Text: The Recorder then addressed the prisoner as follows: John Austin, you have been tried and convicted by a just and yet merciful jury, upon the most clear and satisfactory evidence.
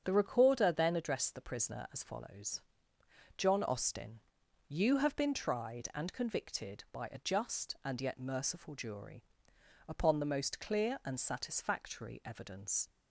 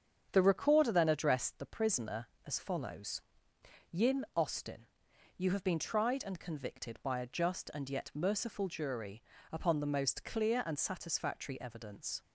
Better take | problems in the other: first | starts louder than the rest; strong; until 1.3 s; 8 dB; strong in the first // says "Yin" for "John"; at 3.8 s

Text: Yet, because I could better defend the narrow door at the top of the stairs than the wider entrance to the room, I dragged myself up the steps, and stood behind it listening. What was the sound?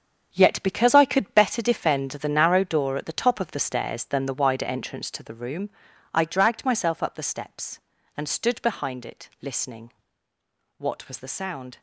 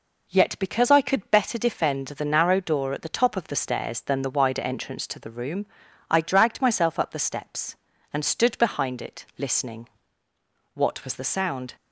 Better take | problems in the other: second | gets quieter; strong; throughout; 11 dB

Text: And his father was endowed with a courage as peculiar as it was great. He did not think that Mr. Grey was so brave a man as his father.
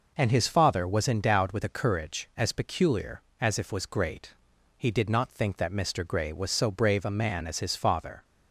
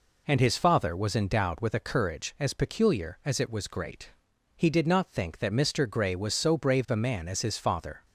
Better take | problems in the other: second | says "if" for "it"; at 3.5 s

